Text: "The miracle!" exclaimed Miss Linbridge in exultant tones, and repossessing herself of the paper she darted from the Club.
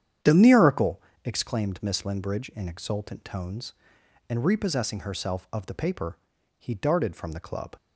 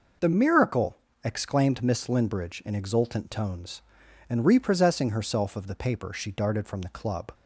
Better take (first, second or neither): second